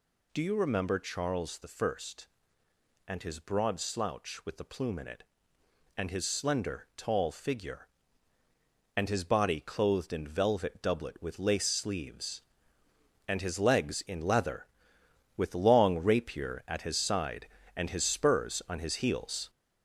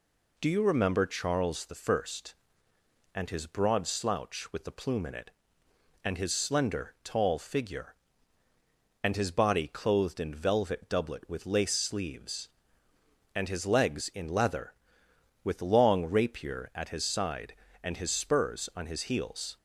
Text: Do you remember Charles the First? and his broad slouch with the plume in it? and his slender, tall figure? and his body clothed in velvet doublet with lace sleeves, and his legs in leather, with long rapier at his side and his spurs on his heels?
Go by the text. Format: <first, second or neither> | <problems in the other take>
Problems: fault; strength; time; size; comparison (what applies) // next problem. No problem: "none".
second | gets louder; noticeable; throughout; 5 dB